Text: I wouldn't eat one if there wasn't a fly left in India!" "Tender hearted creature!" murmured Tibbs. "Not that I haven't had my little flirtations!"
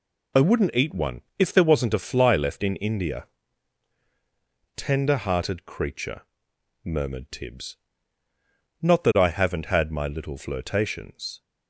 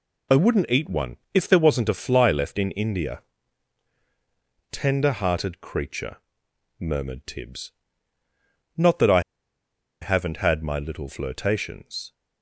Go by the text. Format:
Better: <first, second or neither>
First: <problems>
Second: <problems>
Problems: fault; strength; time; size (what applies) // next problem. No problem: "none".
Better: first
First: pauses between "one" and "if"; slight; at 1.2 s; 0.18 s long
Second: pauses between "one" and "if"; slight; at 1.1 s; 0.18 s long // pauses between "I" and "haven't"; noticeable; at 9.2 s; 0.81 s long